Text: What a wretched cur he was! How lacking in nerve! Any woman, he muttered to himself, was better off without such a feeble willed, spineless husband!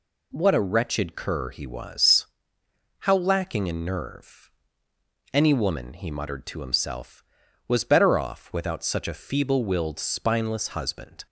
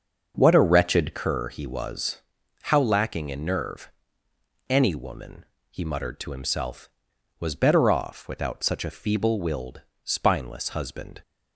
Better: first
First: none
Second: starts louder than the rest; until 1.3 s; 6.5 dB

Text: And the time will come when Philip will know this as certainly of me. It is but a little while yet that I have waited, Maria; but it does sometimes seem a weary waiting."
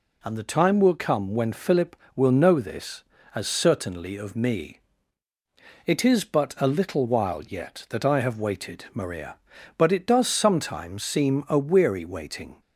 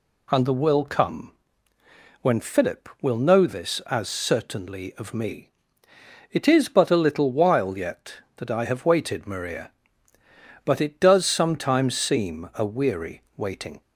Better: first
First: none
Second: skips "time"; at 0.5 s // pauses between "come" and "when"; noticeable; at 1.3 s; 0.88 s long

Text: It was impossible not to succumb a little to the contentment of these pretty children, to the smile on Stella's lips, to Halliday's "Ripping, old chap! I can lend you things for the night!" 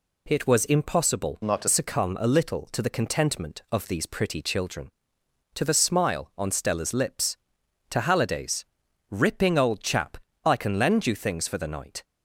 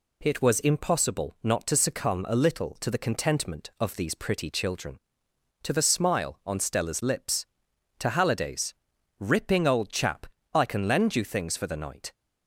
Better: second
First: changes voice from "not" to "to"; from 1.4 to 1.6 s; 0.2 s long // pauses between "Halliday's" and "Ripping"; noticeable; at 8.6 s; 0.46 s long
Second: pauses between "Halliday's" and "Ripping"; noticeable; at 8.7 s; 0.46 s long

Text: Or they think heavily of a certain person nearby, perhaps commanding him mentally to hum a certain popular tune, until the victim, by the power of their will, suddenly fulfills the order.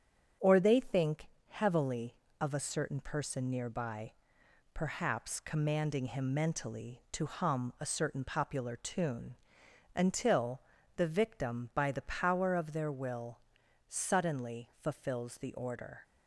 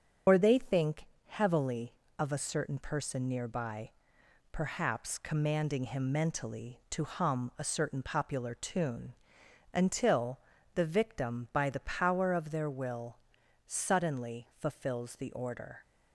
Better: first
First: starts louder than the rest; strong; until 1.6 s; 8 dB // pauses between "think" and "heavily"; slight; at 1.2 s; 0.22 s long // pauses between "until" and "the"; slight; at 10.6 s; 0.34 s long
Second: loses the start of "Or"; at 0.2 s; 80 ms // starts louder than the rest; until 1.4 s; 7 dB // pauses between "think" and "heavily"; slight; at 1.0 s; 0.22 s long // pauses between "until" and "the"; slight; at 10.3 s; 0.34 s long

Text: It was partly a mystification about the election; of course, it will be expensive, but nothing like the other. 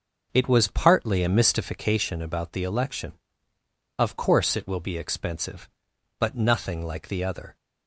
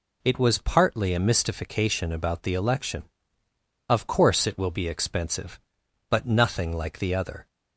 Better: second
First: starts louder than the rest; noticeable; until 2.1 s; 5.5 dB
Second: none

